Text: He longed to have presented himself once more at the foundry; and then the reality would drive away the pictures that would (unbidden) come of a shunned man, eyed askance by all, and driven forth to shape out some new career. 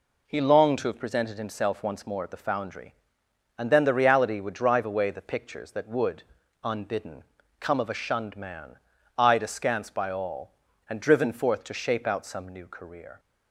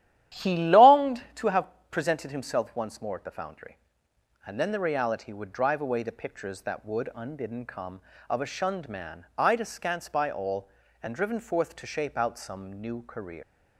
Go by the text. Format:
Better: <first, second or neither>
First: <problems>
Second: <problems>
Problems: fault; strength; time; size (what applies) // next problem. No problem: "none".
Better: first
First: none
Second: starts louder than the rest; strong; until 1.4 s; 12 dB // pauses between "have" and "presented"; slight; at 1.6 s; 0.22 s long // leaves "career" unfinished; at 13.4 s; 135 ms